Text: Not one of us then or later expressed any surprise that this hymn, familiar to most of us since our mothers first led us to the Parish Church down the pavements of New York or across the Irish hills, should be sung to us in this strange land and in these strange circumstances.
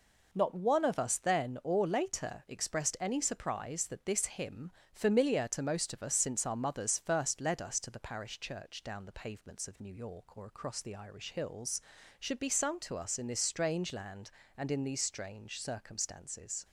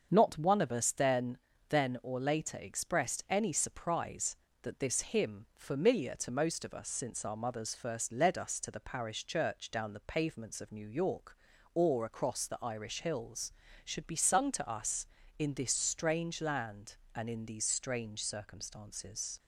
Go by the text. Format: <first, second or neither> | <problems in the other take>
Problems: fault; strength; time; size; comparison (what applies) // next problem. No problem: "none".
first | starts louder than the rest; until 1.1 s; 6.5 dB // says "then" twice; at 1.6 s